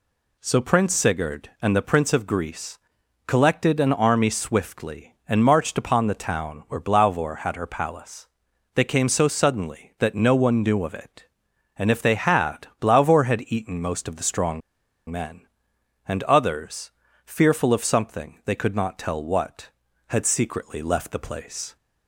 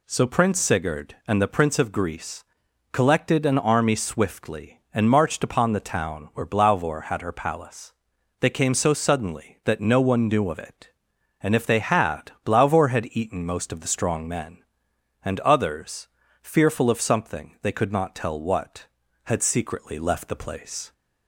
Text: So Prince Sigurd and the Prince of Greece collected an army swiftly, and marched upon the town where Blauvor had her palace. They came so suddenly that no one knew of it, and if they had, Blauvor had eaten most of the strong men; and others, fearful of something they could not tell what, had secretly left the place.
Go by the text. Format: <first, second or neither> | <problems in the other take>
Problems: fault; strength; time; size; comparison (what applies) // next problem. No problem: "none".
second | pauses between "Greece" and "collected"; noticeable; at 2.7 s; 0.48 s long; noticeable in the second // pauses between "strong" and "men"; noticeable; at 14.6 s; 0.49 s long